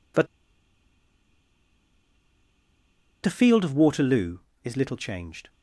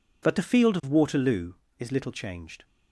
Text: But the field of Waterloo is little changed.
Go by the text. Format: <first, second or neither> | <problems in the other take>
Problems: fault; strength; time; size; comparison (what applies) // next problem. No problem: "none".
second | pauses between "But" and "the"; strong; at 0.2 s; 2.9 s long